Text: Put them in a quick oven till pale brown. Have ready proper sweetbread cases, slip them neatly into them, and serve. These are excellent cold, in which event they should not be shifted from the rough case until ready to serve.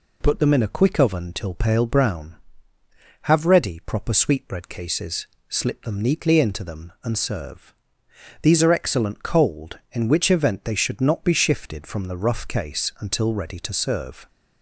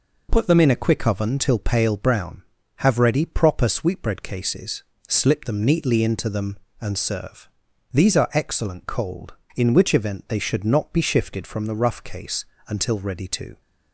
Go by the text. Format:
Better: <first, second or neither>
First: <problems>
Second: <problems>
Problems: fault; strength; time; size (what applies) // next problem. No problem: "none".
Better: first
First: none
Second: pauses between "case" and "until"; slight; at 12.4 s; 0.24 s long // stops before "serve"; at 13.6 s